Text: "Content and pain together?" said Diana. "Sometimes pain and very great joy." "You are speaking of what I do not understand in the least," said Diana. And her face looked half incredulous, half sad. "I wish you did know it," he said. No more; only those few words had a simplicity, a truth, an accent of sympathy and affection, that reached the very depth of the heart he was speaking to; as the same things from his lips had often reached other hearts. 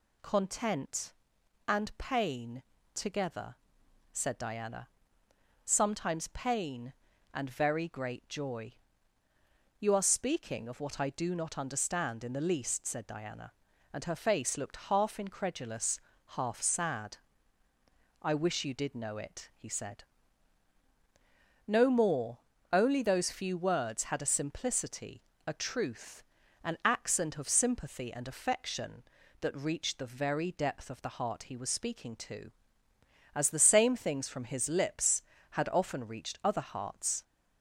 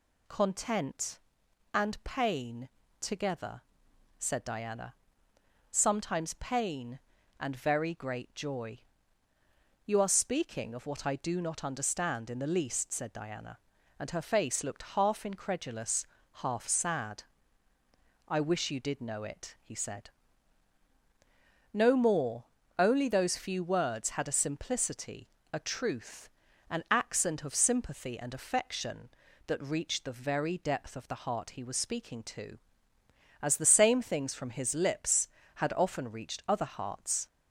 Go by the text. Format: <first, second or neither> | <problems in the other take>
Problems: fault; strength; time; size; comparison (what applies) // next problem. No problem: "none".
neither | pauses between "pain" and "together"; slight; the same in both